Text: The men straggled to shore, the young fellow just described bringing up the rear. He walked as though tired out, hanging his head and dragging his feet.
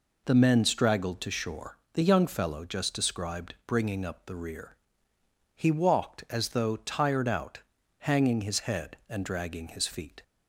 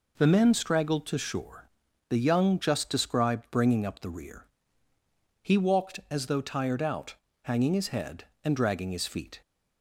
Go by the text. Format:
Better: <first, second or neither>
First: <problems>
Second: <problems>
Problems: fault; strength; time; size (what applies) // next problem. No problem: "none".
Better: first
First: none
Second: skips "fellow"; at 2.5 s